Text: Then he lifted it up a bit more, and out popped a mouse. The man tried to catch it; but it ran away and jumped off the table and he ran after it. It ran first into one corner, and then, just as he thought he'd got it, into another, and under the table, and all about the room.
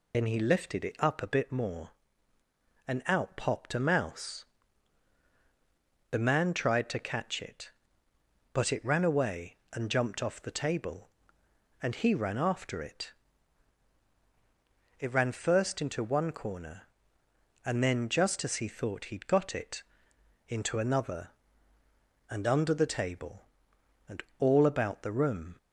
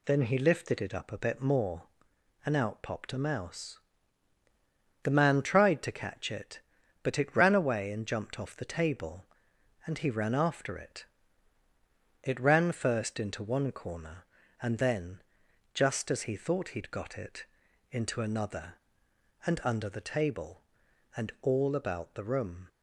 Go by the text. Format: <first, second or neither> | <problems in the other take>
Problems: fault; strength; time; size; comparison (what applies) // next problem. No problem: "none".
second | loses the start of "Then"; at 0.1 s; 60 ms // pauses between "and" and "all"; slight; at 24.2 s; 0.16 s long